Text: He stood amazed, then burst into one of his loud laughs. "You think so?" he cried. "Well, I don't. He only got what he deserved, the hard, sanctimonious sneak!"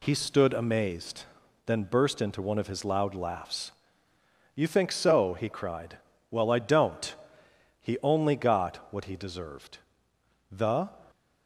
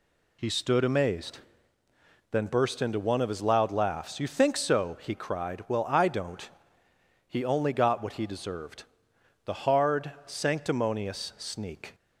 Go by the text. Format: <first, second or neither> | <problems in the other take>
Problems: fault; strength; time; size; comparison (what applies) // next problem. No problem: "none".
second | stops before "hard sanctimonious sneak"; at 11.1 s